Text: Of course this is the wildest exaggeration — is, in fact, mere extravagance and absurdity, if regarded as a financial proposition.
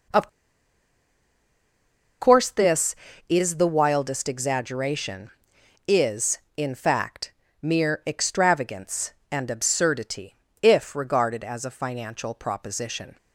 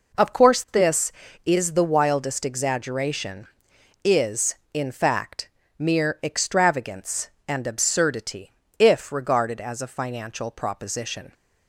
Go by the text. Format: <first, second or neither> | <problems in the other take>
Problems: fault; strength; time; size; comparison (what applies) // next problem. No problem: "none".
second | pauses between "Of" and "course"; strong; at 0.2 s; 1.9 s long